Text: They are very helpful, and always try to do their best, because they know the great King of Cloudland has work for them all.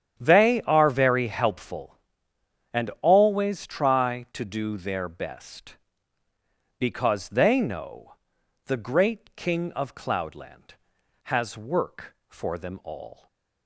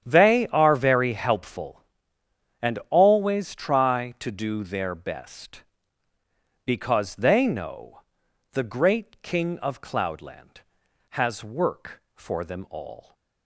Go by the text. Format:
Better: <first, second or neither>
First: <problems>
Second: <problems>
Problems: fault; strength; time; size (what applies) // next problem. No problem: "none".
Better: neither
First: starts louder than the rest; strong; until 1.1 s; 9.5 dB // pauses between "know" and "the"; noticeable; at 8.1 s; 0.50 s long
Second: starts louder than the rest; strong; until 1.0 s; 9.5 dB // pauses between "know" and "the"; noticeable; at 8.0 s; 0.50 s long